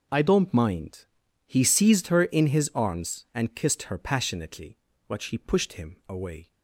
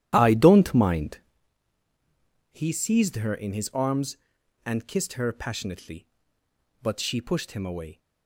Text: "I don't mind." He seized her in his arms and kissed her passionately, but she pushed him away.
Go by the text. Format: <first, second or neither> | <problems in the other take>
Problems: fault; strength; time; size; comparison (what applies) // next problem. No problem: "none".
first | starts louder than the rest; strong; until 1.4 s; 12 dB